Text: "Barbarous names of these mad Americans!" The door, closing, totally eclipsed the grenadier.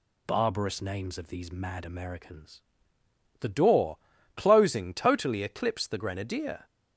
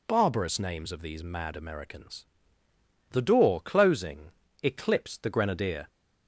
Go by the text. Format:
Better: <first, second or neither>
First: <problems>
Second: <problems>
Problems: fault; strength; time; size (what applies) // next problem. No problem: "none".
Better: first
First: none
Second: skips "totally"; at 4.4 s